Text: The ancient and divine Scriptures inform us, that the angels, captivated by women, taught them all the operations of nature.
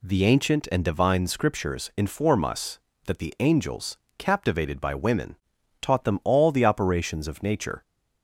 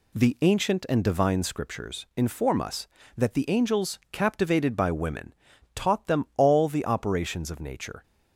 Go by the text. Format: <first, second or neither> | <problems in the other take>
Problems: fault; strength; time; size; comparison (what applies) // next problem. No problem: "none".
neither | none